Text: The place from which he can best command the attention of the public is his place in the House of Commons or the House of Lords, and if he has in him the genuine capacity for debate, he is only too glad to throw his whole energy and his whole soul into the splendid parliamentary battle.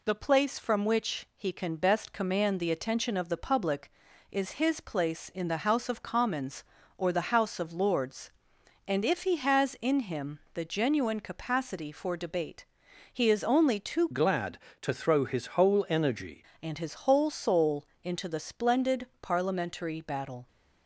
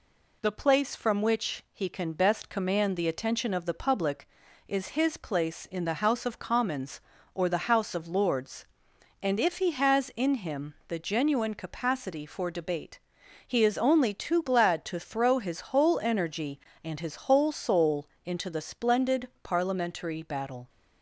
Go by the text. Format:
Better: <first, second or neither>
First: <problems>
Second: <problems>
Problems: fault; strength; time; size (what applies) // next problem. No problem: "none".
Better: second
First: changes voice from "glad" to "energy"; from 14.1 to 16.4 s; 2.3 s long // pauses between "soul" and "into"; slight; at 17.8 s; 0.22 s long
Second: pauses between "soul" and "into"; slight; at 18.0 s; 0.22 s long